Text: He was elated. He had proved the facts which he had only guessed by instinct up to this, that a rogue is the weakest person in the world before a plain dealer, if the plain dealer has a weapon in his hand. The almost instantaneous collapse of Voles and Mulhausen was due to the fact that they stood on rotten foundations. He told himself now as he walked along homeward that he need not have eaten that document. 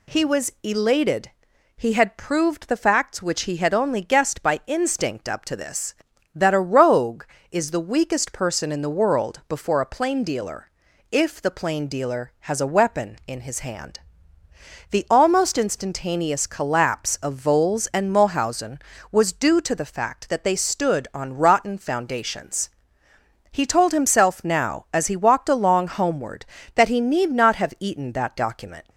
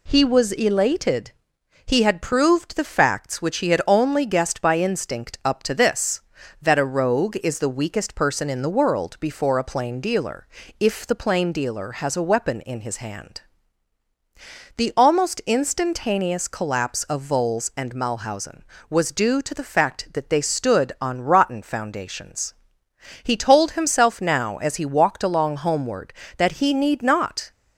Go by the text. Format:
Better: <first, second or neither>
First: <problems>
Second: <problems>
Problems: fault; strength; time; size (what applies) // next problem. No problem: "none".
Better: first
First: none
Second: stops before "have eaten that document"; at 27.5 s